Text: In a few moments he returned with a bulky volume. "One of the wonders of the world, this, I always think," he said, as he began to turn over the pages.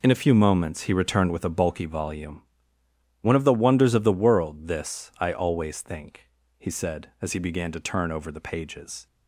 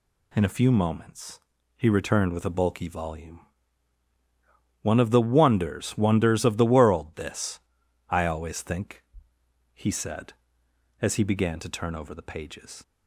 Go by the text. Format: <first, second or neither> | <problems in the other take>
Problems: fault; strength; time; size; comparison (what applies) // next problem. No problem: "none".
first | pauses between "moments" and "he"; slight; at 1.4 s; 0.36 s long // says "wonders" twice; at 5.9 s